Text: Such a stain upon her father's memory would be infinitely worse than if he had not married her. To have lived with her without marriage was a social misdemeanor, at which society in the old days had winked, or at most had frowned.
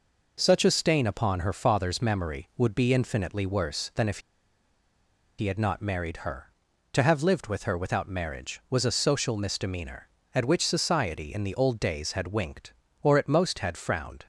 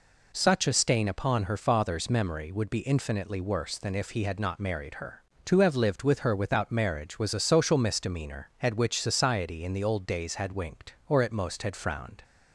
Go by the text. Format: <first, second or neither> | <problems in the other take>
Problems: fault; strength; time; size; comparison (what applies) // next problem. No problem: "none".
second | pauses between "if" and "he"; at 4.1 s; 1.1 s long